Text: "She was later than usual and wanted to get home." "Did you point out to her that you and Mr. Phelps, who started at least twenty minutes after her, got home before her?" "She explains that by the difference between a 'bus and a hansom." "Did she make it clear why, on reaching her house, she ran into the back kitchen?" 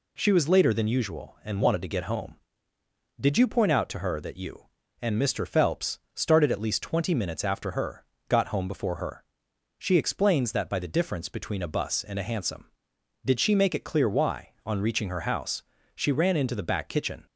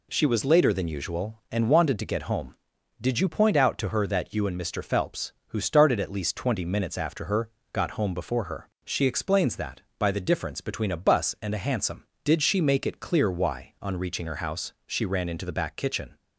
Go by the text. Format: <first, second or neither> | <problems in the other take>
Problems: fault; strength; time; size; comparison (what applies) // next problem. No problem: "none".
second | skips "who"; at 6.0 s